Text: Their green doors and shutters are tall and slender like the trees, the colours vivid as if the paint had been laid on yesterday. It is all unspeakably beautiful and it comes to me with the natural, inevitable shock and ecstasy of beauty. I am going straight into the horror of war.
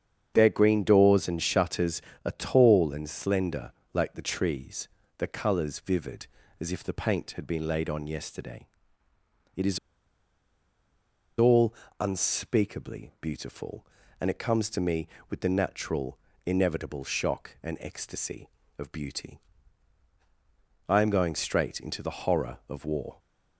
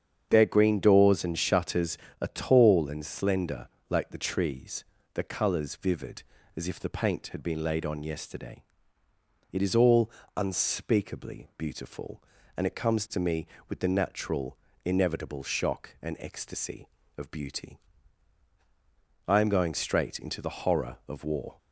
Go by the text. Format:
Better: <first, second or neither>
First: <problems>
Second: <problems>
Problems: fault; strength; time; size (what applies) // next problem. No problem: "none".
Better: second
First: starts louder than the rest; strong; until 1.3 s; 8 dB // pauses between "slender" and "like"; slight; at 3.7 s; 0.22 s long // pauses between "is" and "all"; strong; at 9.7 s; 1.5 s long // pauses between "all" and "unspeakably"; slight; at 11.7 s; 0.26 s long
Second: starts louder than the rest; strong; until 1.3 s; 8 dB // pauses between "slender" and "like"; slight; at 3.6 s; 0.22 s long // pauses between "all" and "unspeakably"; slight; at 10.0 s; 0.26 s long